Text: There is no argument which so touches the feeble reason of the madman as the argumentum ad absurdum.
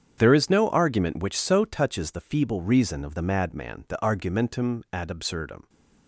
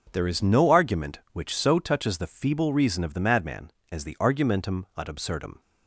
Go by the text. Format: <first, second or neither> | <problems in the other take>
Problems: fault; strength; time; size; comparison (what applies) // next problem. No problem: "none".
second | starts louder than the rest; strong; until 1.1 s; 8.5 dB // skips "as"; at 3.8 s